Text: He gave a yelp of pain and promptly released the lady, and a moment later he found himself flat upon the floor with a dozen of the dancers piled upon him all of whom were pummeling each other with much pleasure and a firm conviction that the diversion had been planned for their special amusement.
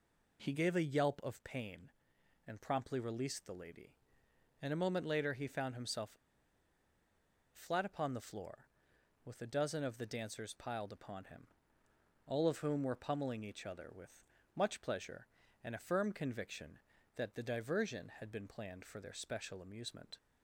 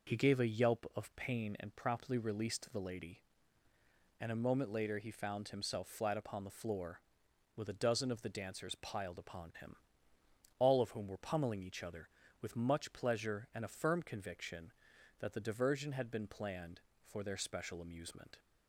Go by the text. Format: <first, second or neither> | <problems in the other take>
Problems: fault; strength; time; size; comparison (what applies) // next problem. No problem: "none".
second | pauses between "himself" and "flat"; strong; at 6.1 s; 1.3 s long // pauses between "him" and "all"; noticeable; at 11.4 s; 0.76 s long; noticeable in the second // pauses between "with" and "much"; slight; at 14.2 s; 0.30 s long